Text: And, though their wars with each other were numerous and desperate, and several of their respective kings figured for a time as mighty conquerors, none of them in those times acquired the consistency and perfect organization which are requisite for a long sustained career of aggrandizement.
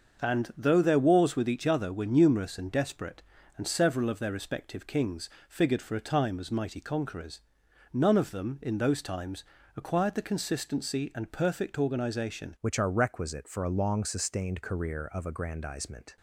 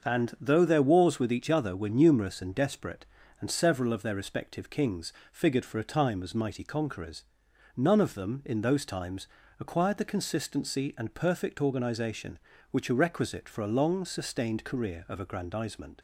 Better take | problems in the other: second | starts louder than the rest; until 1.2 s; 6.5 dB; also in the second // pauses between "kings" and "figured"; slight; at 5.2 s; 0.18 s long; slight in the second // pauses between "times" and "acquired"; slight; at 9.4 s; 0.34 s long; slight in the second // changes voice at "which"; from 12.6 s on; 3.5 s long

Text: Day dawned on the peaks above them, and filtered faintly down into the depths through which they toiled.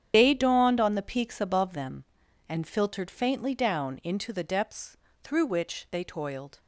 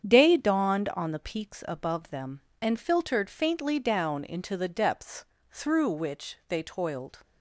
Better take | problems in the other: second | loses the start of "Day"; at 0.1 s; 80 ms // starts louder than the rest; strong; until 1.1 s; 8.5 dB; strong in the second // pauses between "depths" and "through"; slight; at 4.9 s; 0.26 s long; slight in the second

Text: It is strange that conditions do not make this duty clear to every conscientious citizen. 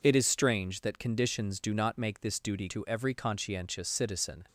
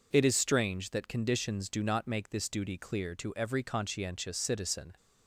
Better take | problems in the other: second | skips "clear"; at 2.6 s

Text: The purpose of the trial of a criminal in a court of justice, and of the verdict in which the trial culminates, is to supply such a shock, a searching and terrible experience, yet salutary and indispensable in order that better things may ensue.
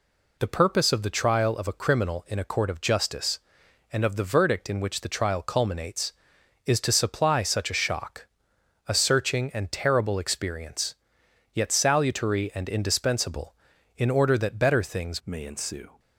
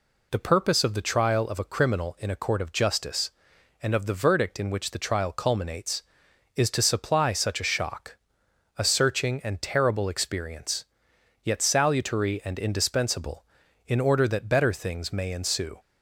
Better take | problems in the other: second | changes voice at "may"; from 15.2 s on; 0.7 s long

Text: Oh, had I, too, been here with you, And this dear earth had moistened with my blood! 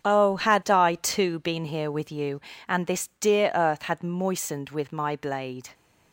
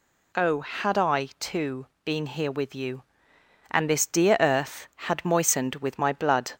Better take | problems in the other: second | starts louder than the rest; strong; until 1.1 s; 8.5 dB // says "blade" for "blood"; at 5.1 s

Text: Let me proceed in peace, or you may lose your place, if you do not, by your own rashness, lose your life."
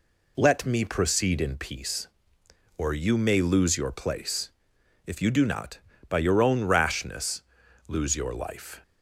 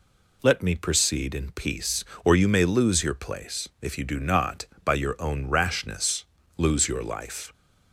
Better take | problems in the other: neither | none

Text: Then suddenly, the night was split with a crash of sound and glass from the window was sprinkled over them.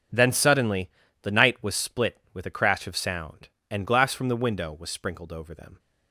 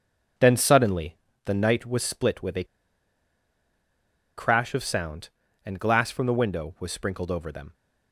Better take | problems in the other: first | pauses between "a" and "crash"; strong; at 2.6 s; 1.7 s long

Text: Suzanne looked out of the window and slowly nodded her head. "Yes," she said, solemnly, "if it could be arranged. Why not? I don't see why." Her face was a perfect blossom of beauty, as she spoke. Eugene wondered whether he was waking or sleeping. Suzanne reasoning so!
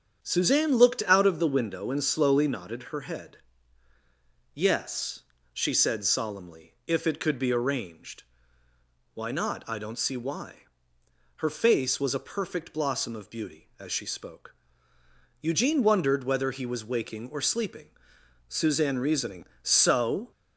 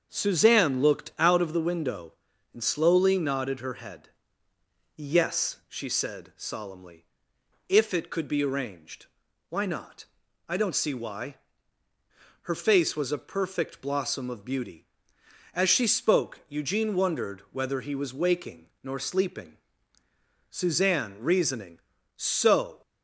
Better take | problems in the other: first | starts louder than the rest; until 1.1 s; 7 dB; strong in the first // says "nor" for "or"; at 18.8 s

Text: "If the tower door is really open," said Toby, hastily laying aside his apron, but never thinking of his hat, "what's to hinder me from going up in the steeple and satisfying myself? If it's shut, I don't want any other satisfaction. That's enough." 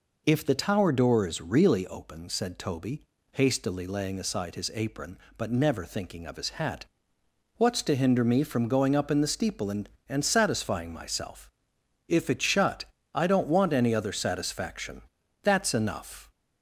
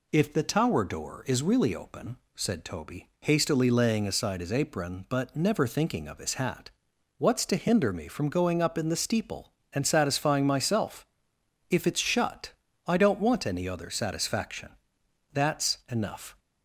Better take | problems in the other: second | says "and" twice; at 10.0 s

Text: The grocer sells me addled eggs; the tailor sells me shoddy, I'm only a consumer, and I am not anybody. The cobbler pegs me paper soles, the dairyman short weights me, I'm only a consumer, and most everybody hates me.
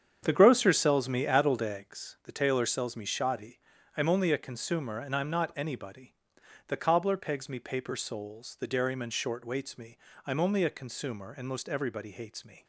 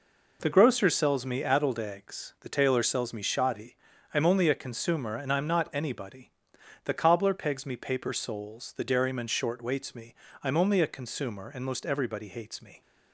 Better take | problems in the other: second | starts louder than the rest; strong; until 1.9 s; 8 dB

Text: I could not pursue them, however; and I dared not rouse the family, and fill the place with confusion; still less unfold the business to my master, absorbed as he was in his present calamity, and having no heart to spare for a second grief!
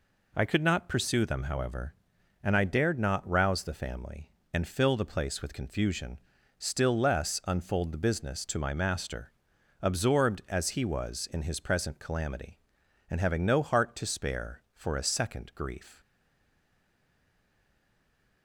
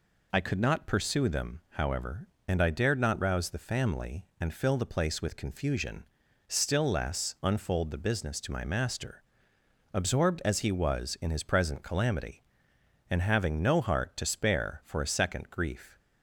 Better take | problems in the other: second | stays silent after the last word; from 16.0 s on; 2.4 s long

